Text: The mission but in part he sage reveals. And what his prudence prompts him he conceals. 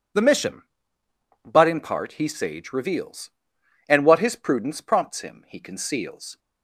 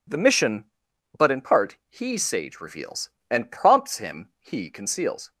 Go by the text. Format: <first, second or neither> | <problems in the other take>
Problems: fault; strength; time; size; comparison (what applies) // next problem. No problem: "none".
first | skips "what his prudence"; at 3.5 s